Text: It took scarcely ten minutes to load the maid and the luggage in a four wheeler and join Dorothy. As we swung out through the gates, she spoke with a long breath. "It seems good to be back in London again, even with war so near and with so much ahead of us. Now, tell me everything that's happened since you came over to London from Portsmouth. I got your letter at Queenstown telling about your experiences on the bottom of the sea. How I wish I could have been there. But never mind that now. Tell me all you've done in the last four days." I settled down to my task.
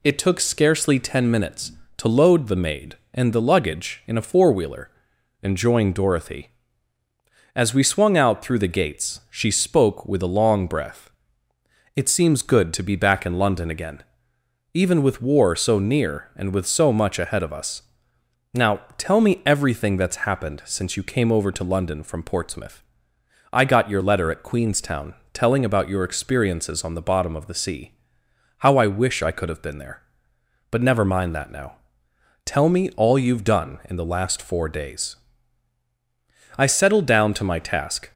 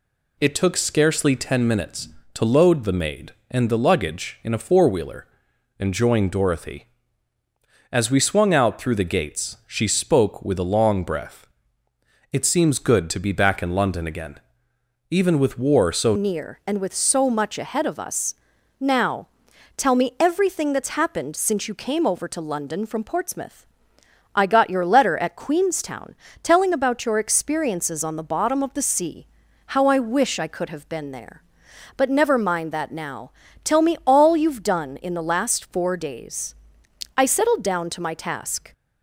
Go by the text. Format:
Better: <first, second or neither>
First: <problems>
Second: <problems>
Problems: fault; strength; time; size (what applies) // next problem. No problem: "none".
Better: first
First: pauses between "Queenstown" and "telling"; slight; at 25.1 s; 0.20 s long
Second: changes voice at "near"; from 16.1 s on; 22.6 s long // pauses between "Queenstown" and "telling"; slight; at 26.1 s; 0.28 s long